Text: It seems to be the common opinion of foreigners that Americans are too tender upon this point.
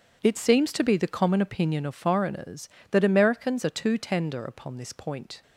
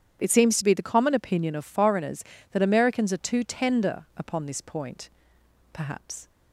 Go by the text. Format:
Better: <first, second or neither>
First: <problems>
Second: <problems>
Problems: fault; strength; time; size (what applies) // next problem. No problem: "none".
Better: first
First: none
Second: starts louder than the rest; strong; until 1.2 s; 9.5 dB // goes on to say "Perhaps"; from 5.7 s on; 0.56 s long